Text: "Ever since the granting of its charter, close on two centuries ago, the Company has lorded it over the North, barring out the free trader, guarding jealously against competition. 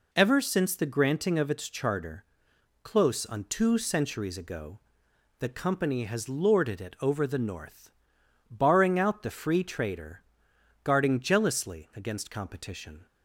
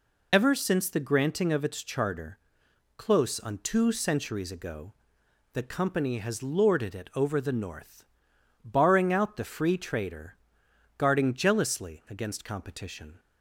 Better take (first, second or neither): first